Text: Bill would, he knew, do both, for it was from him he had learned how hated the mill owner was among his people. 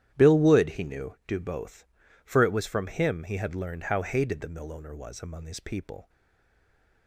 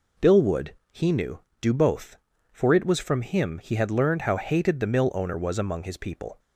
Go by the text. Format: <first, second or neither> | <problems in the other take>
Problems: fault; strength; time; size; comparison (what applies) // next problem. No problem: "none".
second | starts louder than the rest; strong; until 1.1 s; 11 dB // stays silent after the last word; from 6.0 s on; 1.0 s long